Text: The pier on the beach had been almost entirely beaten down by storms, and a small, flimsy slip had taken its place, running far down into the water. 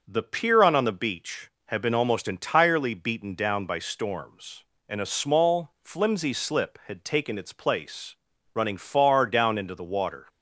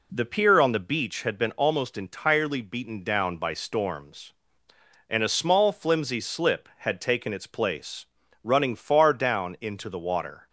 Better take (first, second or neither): second